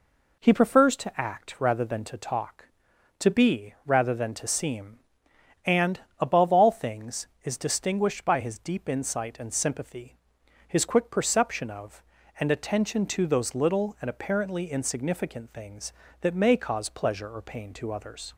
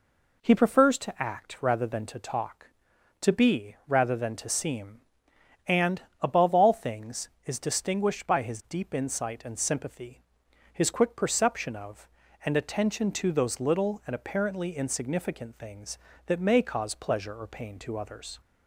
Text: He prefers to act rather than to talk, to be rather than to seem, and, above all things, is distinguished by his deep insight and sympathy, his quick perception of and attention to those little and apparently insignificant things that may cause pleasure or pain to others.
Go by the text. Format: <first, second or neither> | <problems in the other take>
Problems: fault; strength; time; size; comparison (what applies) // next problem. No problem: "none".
neither | none